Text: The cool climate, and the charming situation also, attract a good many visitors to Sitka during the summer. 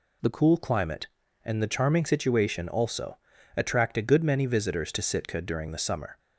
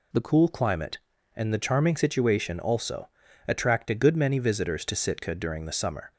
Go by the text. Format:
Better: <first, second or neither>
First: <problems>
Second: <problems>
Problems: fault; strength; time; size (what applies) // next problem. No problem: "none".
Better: neither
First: none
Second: none